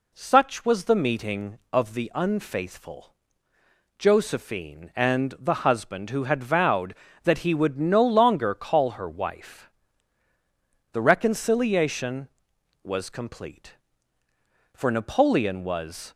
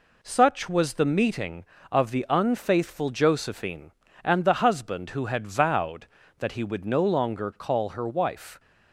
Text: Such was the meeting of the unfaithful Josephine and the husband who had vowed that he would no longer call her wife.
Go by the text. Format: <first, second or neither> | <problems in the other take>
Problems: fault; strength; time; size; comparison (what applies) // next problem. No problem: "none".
second | pauses between "unfaithful" and "Josephine"; noticeable; at 3.1 s; 0.82 s long // goes on to say "The reconciliation was complete for Napoleon was"; strong; from 10.9 s on; 5.2 s long